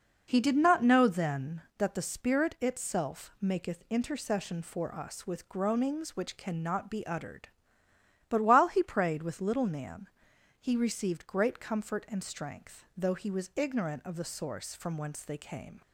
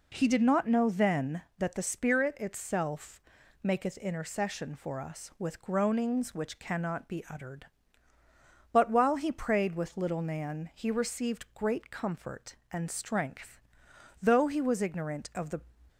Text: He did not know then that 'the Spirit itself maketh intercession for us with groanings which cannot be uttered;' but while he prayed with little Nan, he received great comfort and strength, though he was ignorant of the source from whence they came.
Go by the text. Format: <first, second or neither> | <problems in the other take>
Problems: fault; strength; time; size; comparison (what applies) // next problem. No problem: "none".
first | pauses between "itself" and "maketh"; at 3.2 s; 0.40 s long // stops before "source from whence they came"; at 15.8 s